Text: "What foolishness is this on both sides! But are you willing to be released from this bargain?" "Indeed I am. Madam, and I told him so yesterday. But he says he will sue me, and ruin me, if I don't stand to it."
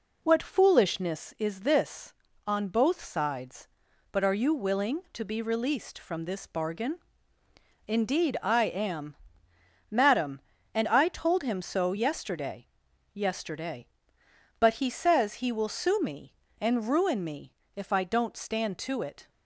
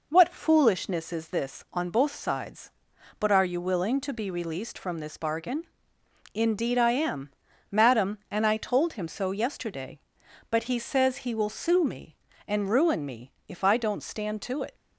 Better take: second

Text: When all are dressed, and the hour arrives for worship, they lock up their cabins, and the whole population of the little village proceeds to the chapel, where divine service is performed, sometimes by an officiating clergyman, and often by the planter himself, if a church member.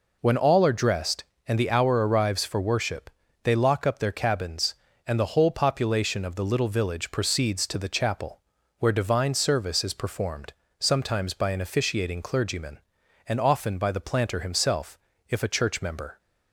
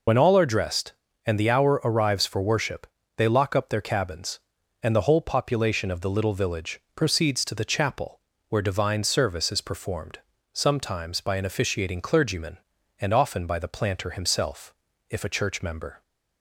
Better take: first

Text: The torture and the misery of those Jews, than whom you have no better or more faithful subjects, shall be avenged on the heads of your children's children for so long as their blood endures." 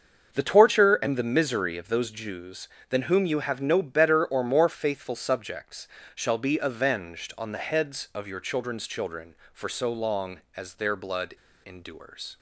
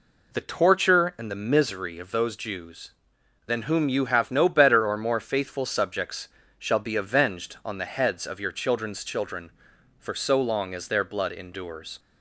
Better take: second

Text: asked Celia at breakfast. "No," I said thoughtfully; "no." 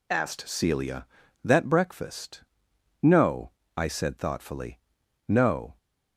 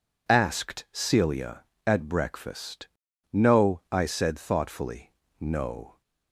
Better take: second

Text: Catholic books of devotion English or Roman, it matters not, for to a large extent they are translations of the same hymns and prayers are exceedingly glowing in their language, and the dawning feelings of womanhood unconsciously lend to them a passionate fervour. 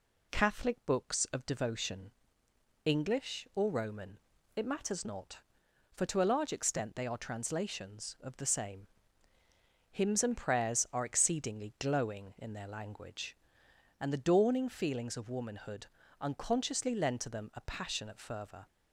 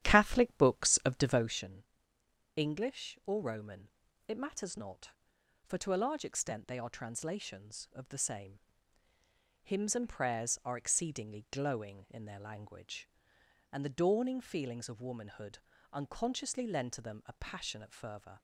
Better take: first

